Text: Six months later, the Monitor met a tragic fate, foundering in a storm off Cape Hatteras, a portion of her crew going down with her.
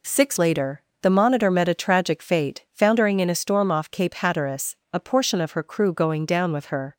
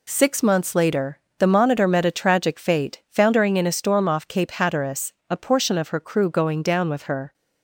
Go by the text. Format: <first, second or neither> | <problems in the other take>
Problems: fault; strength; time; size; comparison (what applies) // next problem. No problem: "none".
second | skips "months"; at 0.3 s